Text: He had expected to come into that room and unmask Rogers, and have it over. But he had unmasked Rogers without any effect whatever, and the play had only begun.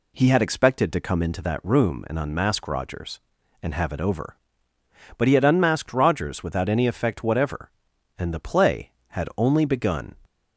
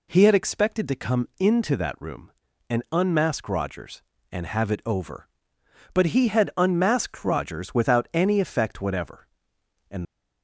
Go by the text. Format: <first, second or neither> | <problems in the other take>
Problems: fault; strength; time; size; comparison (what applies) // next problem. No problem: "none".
first | stops before "the play had only begun"; at 10.0 s